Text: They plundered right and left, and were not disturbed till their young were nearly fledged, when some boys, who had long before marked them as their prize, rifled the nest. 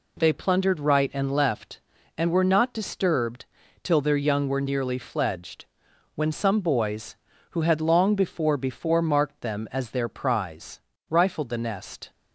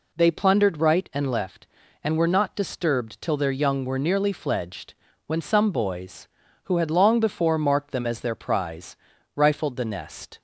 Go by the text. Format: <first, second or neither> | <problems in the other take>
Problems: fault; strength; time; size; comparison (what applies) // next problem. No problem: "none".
second | pauses between "disturbed" and "till"; at 3.4 s; 0.38 s long // says "before" twice; at 8.5 s